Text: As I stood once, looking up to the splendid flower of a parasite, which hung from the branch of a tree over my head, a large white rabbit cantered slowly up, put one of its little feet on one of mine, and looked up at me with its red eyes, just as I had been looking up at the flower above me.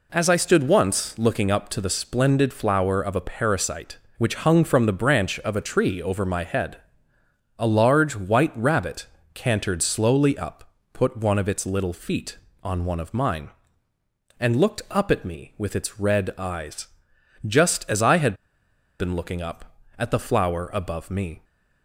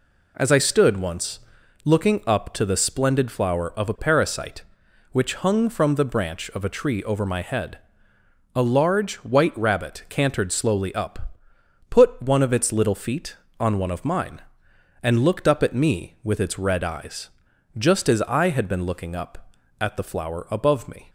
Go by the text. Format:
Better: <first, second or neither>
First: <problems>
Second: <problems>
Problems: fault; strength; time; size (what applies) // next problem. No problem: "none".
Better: second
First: pauses between "rabbit" and "cantered"; slight; at 9.0 s; 0.28 s long // pauses between "had" and "been"; noticeable; at 18.3 s; 0.64 s long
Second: none